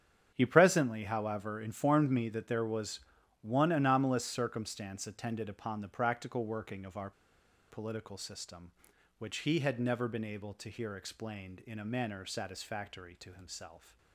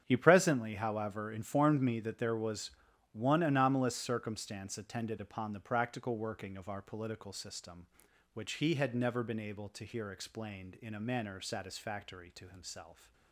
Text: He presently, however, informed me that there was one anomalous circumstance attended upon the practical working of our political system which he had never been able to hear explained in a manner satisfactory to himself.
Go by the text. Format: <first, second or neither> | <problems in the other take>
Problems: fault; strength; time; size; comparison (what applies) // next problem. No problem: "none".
second | starts louder than the rest; strong; until 1.3 s; 8.5 dB; strong in the second // pauses between "was" and "one"; at 2.9 s; 0.44 s long; also in the second // pauses between "our" and "political"; noticeable; at 7.1 s; 0.59 s long